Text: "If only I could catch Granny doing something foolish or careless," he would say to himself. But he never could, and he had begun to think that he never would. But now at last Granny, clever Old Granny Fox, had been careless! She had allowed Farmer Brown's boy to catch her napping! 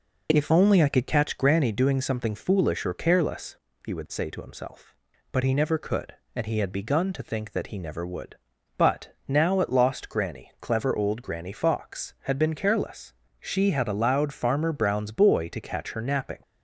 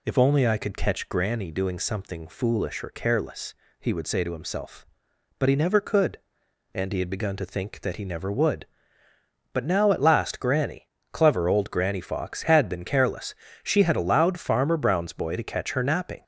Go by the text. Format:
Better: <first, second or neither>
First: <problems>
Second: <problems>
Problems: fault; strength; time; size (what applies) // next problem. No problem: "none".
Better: second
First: says "lost" for "last"; at 9.7 s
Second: none